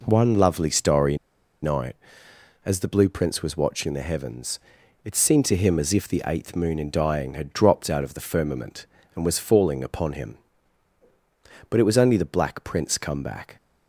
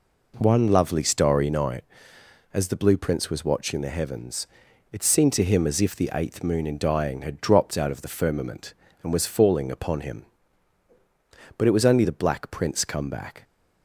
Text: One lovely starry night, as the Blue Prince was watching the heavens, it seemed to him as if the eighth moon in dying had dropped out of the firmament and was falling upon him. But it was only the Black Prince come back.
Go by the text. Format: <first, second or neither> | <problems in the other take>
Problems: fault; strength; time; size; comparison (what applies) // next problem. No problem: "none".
second | pauses between "starry" and "night"; noticeable; at 1.1 s; 0.46 s long